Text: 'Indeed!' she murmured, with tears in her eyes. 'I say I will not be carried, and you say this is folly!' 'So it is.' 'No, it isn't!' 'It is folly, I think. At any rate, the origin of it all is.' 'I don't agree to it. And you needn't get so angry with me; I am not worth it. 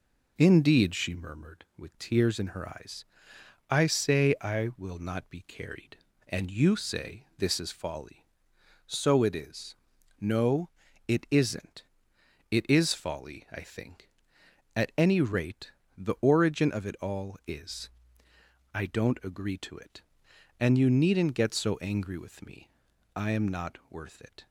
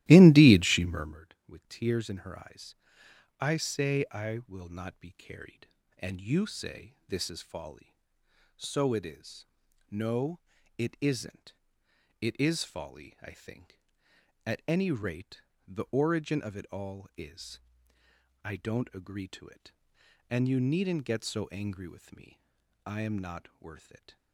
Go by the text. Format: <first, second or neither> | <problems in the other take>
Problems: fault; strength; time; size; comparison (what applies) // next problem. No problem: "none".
first | starts louder than the rest; strong; until 1.2 s; 15.5 dB